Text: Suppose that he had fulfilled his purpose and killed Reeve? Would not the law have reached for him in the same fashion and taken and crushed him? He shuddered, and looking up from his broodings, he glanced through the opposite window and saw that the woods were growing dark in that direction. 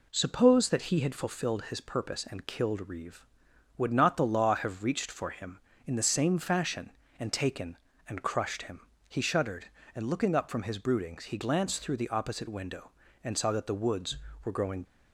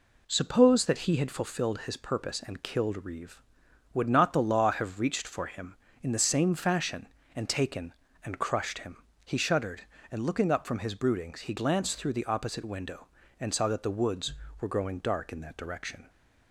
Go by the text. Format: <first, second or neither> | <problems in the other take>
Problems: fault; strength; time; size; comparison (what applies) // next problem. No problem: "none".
second | stops before "dark in that direction"; at 14.8 s